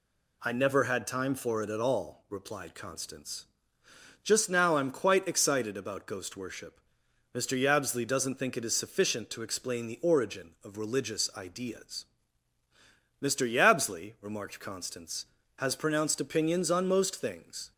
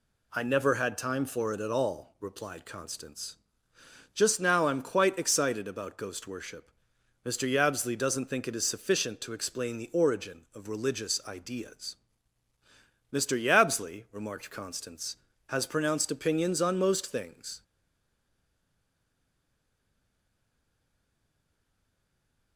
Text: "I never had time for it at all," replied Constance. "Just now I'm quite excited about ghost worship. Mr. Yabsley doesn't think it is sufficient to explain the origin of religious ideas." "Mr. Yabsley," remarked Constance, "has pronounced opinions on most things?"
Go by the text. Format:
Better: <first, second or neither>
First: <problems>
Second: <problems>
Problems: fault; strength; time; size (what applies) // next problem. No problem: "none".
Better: first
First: none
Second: stays silent after the last word; strong; from 17.6 s on; 4.9 s long